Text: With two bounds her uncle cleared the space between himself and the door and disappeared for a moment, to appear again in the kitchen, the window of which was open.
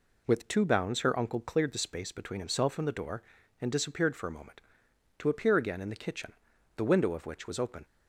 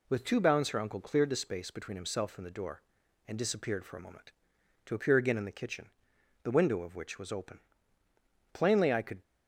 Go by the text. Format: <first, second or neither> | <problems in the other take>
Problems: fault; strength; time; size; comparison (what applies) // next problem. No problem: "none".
first | goes on to say "Plainly I could"; noticeable; from 8.5 s on; 0.68 s long